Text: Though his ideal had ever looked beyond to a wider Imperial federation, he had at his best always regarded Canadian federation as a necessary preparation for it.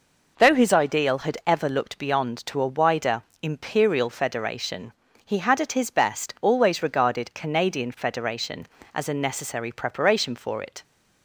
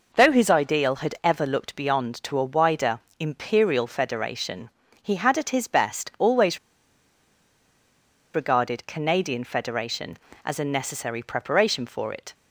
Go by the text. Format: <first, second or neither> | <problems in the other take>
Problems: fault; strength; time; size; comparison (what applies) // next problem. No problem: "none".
first | pauses between "wider" and "Imperial"; slight; at 3.0 s; 0.18 s long; slight in the first // pauses between "always" and "regarded"; strong; at 6.5 s; 1.7 s long